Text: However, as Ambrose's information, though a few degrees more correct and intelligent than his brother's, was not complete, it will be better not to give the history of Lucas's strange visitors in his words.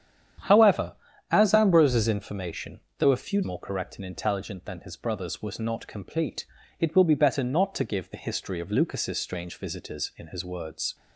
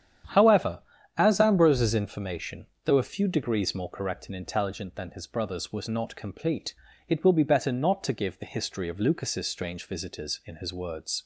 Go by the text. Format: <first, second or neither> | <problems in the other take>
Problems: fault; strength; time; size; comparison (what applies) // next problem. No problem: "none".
second | starts louder than the rest; strong; until 1.8 s; 9.5 dB; strong in the second // skips "degrees"; at 3.4 s